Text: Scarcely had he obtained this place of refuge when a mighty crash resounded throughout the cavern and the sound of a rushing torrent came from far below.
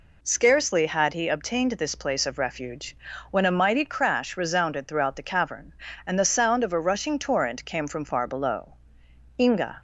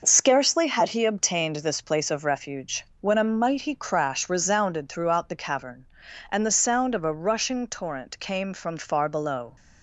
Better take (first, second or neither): second